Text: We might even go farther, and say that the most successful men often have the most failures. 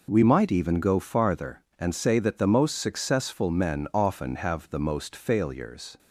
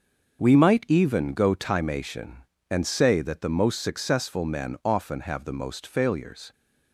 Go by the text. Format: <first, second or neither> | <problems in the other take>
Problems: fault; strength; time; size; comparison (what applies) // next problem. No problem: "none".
first | starts louder than the rest; until 1.4 s; 6.5 dB // says "timation" for "farther"; at 1.5 s